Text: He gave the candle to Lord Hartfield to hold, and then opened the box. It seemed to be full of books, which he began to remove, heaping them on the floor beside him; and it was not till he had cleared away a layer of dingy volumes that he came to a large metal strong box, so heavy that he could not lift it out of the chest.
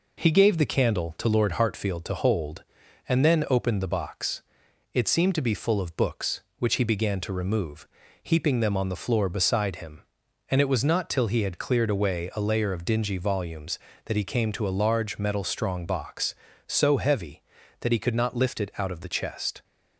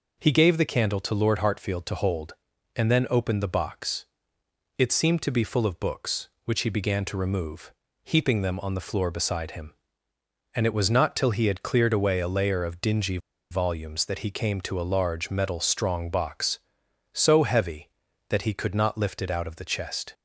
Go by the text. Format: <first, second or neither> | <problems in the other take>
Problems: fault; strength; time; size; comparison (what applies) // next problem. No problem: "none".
first | pauses between "dingy" and "volumes"; slight; at 13.1 s; 0.33 s long